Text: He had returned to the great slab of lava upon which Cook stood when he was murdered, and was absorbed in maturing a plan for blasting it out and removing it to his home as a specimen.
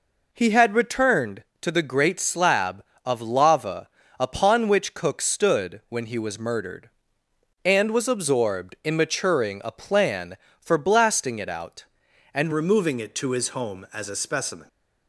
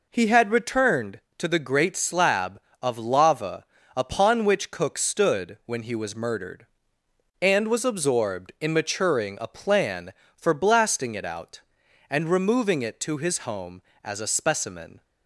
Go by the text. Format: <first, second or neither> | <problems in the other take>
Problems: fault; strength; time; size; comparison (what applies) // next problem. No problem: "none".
second | pauses between "lava" and "upon"; slight; at 3.8 s; 0.32 s long; slight in the second // changes voice at "removing"; from 12.5 s on; 2.1 s long